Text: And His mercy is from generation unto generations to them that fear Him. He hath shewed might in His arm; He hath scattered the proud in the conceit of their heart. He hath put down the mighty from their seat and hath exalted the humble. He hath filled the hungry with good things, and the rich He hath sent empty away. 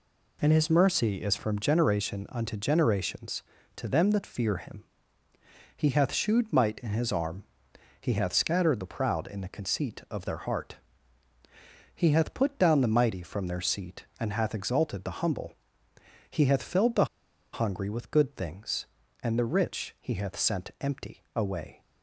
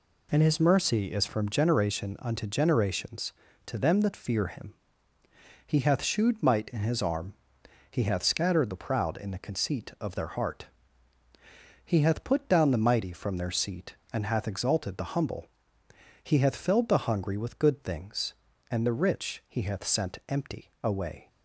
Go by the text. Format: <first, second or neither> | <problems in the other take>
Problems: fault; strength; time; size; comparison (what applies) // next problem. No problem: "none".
second | pauses between "the" and "hungry"; noticeable; at 17.0 s; 0.47 s long